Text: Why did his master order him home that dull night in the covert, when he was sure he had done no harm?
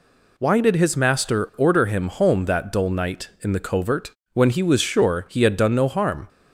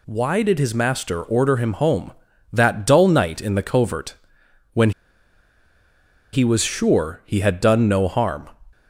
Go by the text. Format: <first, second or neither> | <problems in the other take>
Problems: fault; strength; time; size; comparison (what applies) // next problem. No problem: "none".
first | pauses between "when" and "he"; strong; at 4.9 s; 1.4 s long